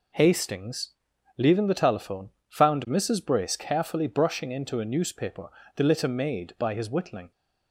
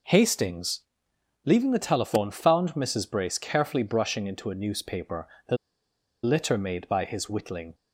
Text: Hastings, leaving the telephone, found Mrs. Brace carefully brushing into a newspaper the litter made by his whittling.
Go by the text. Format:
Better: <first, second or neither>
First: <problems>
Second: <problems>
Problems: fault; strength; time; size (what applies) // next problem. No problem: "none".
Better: first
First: pauses between "newspaper" and "the"; slight; at 5.4 s; 0.26 s long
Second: pauses between "newspaper" and "the"; slight; at 5.2 s; 0.20 s long // pauses between "the" and "litter"; noticeable; at 5.5 s; 0.67 s long